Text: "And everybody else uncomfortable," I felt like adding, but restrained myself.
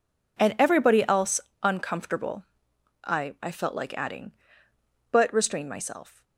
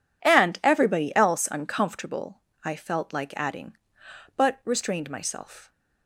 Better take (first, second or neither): second